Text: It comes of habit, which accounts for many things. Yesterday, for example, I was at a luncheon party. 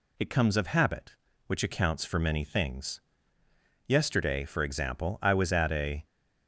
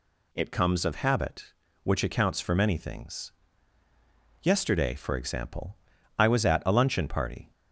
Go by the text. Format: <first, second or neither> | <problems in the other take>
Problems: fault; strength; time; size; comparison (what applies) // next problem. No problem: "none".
second | stops before "luncheon party"; at 6.0 s